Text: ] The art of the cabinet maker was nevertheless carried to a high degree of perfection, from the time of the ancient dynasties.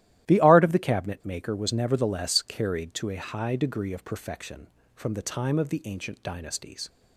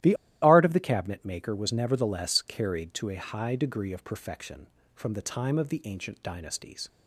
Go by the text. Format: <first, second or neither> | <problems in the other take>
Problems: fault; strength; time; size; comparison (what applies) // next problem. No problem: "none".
first | starts louder than the rest; strong; until 1.3 s; 13.5 dB; strong in the first // pauses between "The" and "art"; slight; at 0.1 s; 0.28 s long